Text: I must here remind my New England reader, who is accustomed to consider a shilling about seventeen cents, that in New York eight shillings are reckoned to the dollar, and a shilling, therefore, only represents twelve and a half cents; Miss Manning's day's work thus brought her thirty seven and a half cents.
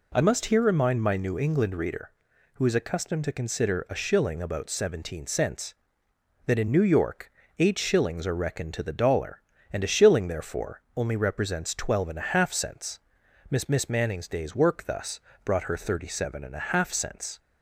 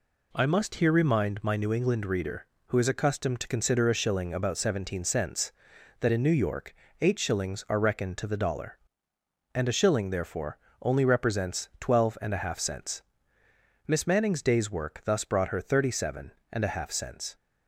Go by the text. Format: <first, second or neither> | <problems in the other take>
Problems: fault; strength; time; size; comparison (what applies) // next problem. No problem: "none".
second | pauses between "York" and "eight"; slight; at 7.3 s; 0.28 s long; slight in the second // says "Miss" twice; at 13.6 s // pauses between "thus" and "brought"; slight; at 15.2 s; 0.24 s long